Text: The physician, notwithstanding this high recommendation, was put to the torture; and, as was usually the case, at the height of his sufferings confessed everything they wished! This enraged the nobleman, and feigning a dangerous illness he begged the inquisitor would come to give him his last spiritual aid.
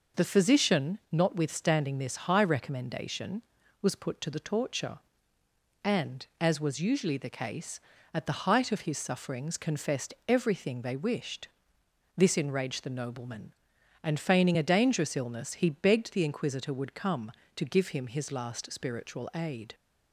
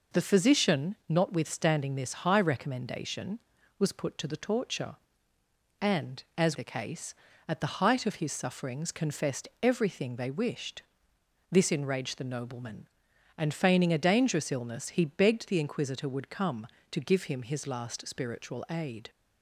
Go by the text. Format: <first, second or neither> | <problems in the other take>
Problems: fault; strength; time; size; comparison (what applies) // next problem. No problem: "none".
first | skips "was usually"; at 6.5 s